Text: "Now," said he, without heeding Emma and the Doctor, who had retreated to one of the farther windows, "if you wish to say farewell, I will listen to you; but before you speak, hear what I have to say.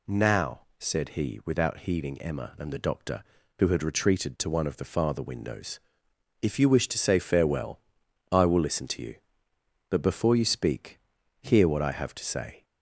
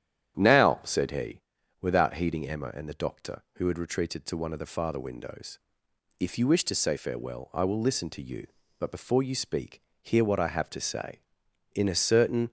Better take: first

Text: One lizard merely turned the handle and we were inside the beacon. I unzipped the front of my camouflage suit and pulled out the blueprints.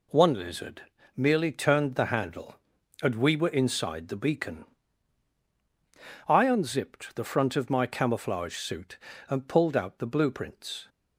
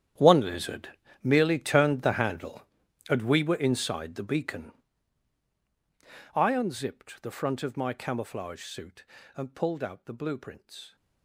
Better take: first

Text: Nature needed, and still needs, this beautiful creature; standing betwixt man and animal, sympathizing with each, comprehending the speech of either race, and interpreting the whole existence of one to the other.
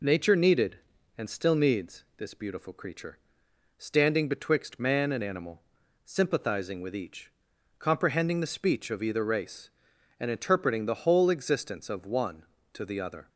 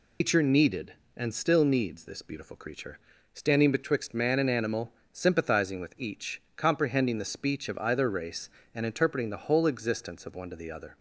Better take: first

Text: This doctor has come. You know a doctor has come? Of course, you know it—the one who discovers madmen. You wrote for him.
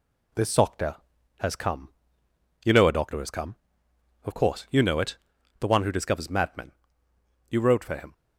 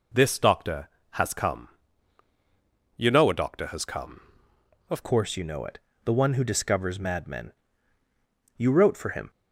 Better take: first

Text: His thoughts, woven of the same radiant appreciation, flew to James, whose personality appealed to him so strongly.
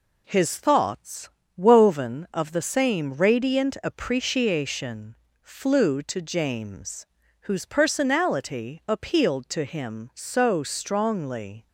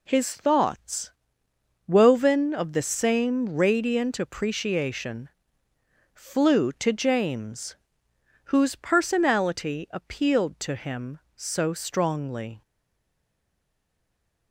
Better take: first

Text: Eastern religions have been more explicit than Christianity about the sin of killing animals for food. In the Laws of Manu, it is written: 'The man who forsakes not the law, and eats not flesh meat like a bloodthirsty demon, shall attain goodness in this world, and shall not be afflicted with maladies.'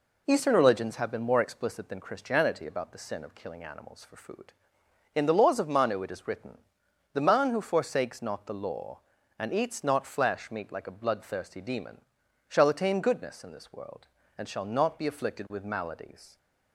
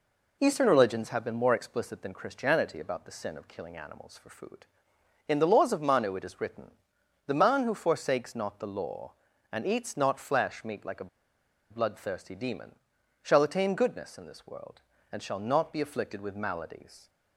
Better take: first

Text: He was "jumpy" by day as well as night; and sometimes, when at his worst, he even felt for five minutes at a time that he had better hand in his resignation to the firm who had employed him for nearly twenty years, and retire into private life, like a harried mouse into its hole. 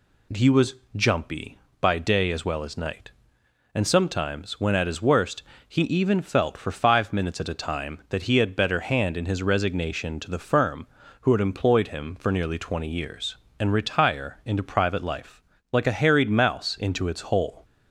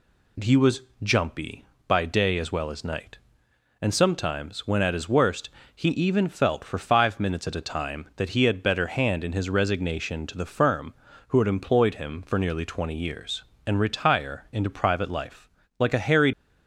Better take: first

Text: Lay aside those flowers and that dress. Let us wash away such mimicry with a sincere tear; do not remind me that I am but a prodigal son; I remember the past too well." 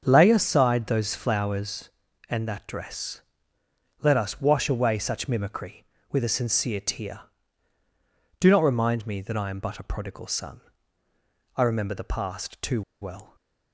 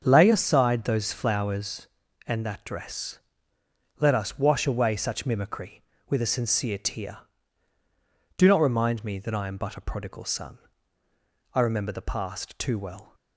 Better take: second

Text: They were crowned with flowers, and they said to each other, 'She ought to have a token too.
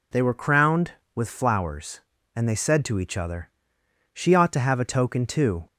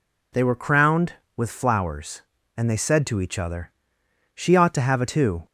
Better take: first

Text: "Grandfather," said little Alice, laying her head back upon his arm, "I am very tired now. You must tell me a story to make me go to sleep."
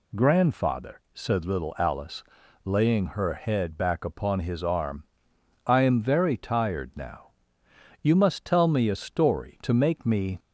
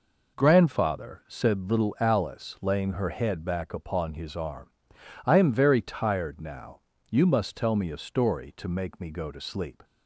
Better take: second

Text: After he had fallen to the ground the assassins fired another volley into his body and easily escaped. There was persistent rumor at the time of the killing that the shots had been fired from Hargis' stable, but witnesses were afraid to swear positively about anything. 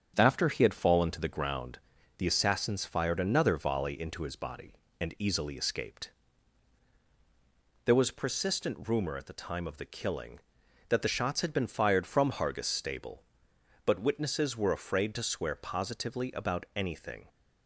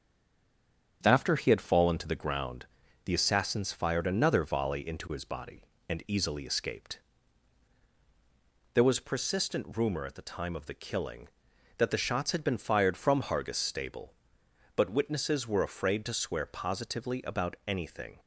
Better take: first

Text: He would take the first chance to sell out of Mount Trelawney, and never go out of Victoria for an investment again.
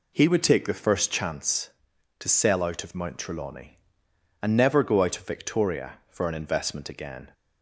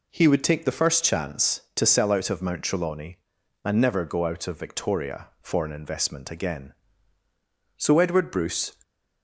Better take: first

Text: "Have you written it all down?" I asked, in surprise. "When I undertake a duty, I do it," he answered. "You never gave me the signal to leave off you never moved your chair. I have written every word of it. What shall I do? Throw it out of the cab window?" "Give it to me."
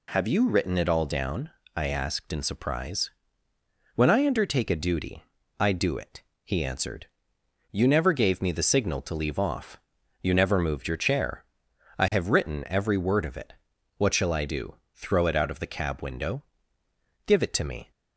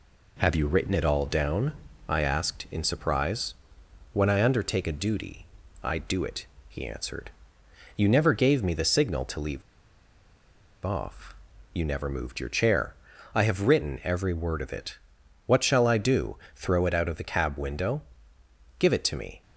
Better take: first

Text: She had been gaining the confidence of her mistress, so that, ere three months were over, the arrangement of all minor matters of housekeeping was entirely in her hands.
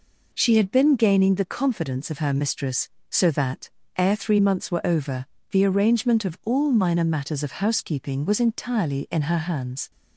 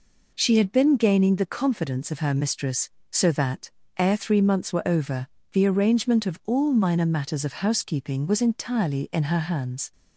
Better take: neither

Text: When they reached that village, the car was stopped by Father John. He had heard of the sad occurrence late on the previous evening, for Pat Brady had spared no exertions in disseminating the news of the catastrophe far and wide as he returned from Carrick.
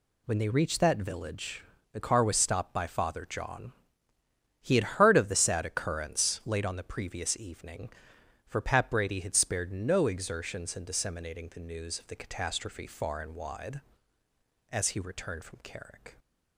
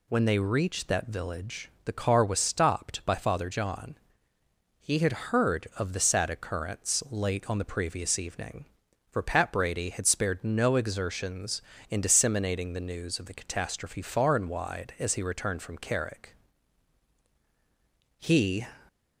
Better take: first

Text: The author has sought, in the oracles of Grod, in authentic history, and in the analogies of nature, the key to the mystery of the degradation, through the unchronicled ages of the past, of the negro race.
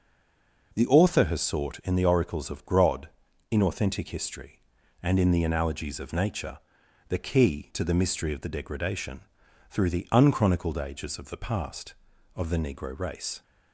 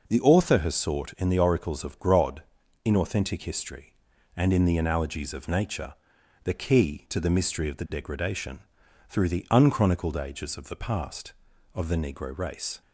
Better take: second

